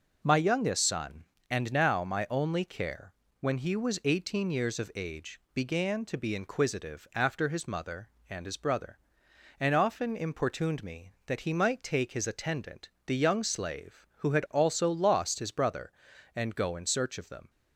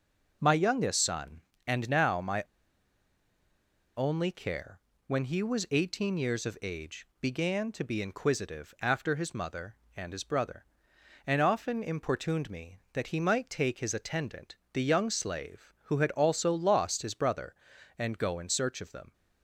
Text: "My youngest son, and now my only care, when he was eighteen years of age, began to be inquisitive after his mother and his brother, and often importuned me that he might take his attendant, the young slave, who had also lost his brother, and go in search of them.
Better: first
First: none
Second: pauses between "my" and "only"; strong; at 2.4 s; 1.5 s long

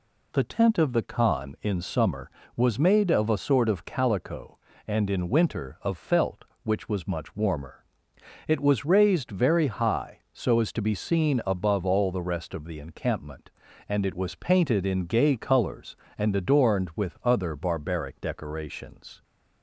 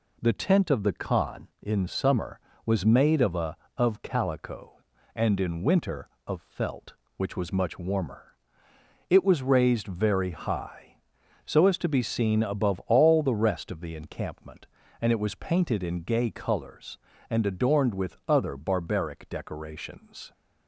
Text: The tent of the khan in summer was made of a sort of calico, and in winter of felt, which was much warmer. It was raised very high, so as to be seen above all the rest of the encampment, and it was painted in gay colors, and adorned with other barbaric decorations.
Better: first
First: none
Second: skips "sort"; at 3.6 s

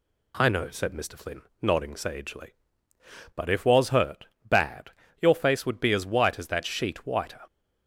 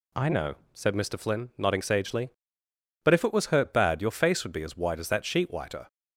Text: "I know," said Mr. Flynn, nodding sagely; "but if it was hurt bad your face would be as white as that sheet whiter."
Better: second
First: skips "it"; at 3.6 s // pauses between "hurt" and "bad"; slight; at 4.2 s; 0.18 s long // pauses between "bad" and "your"; slight; at 4.8 s; 0.32 s long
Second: none

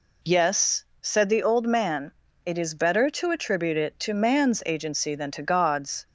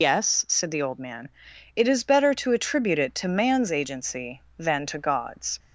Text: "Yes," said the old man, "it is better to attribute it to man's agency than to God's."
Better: first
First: none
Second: loses the start of "Yes"; at 0.0 s; 140 ms

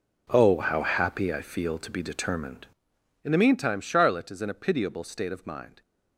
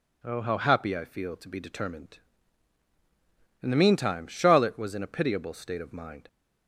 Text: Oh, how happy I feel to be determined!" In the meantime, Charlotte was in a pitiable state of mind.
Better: second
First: says "is" for "was"; at 4.3 s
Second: none

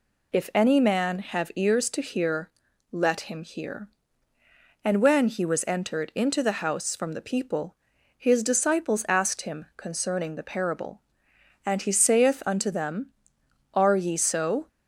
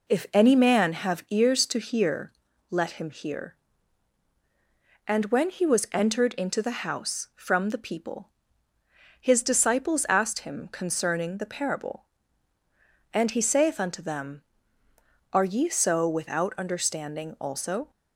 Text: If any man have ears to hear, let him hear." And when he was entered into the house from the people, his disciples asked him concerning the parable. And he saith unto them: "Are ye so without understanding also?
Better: second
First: stops before "without understanding also"; at 14.6 s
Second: none

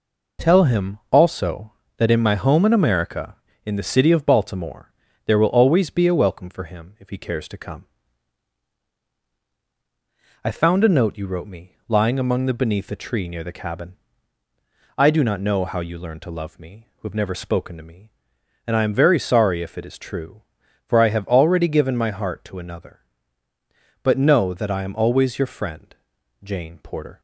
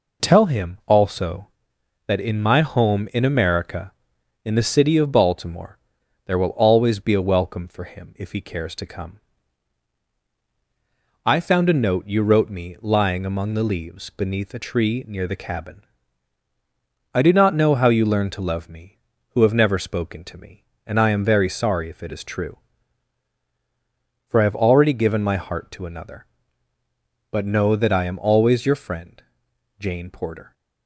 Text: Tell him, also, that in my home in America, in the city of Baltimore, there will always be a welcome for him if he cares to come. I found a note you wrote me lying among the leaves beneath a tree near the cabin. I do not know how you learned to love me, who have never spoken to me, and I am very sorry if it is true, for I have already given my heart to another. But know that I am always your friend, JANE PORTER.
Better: second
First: skips "leaves"; at 12.5 s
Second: none

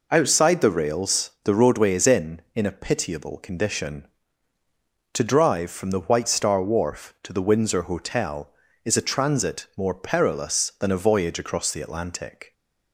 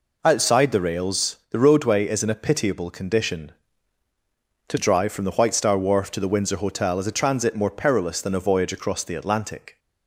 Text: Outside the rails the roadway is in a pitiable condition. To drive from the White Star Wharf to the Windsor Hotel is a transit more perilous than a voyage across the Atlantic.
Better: second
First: says "in" twice; at 2.5 s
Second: none

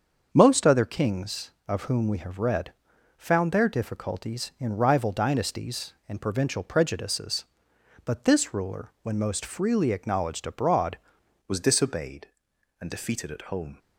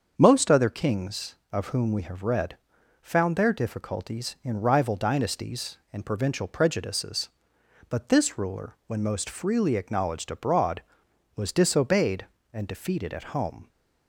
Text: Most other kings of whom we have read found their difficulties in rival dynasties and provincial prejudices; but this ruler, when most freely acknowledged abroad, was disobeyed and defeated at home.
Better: second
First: starts louder than the rest; until 1.3 s; 7 dB // pauses between "read" and "found"; noticeable; at 2.7 s; 0.46 s long // changes voice at "was"; from 11.4 s on; 2.3 s long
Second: starts louder than the rest; until 1.1 s; 7 dB // pauses between "read" and "found"; noticeable; at 2.5 s; 0.46 s long

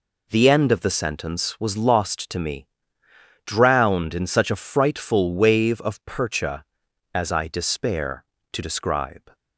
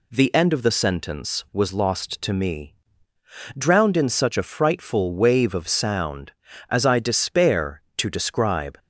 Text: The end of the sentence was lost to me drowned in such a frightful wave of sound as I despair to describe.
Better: second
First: pauses between "me" and "drowned"; noticeable; at 2.6 s; 0.80 s long // says "percha" for "sound"; at 6.0 s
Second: pauses between "me" and "drowned"; noticeable; at 2.7 s; 0.84 s long

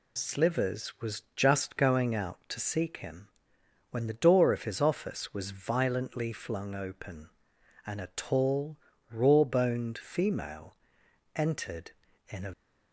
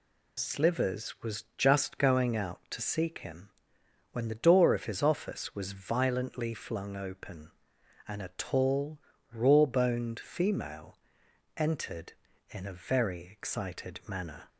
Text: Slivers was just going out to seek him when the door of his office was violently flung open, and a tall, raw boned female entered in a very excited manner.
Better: second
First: pauses between "him" and "when"; noticeable; at 3.2 s; 0.64 s long // pauses between "female" and "entered"; noticeable; at 10.7 s; 0.60 s long // stops before "very excited manner"; at 12.5 s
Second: pauses between "him" and "when"; noticeable; at 3.4 s; 0.64 s long // pauses between "female" and "entered"; noticeable; at 10.9 s; 0.60 s long

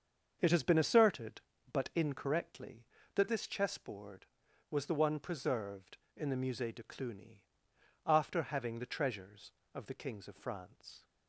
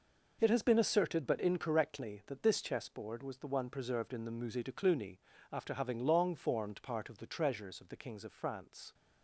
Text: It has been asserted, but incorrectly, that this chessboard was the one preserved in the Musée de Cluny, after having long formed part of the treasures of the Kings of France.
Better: second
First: starts louder than the rest; until 1.4 s; 7 dB // skips "long formed part of"; at 8.7 s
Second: none

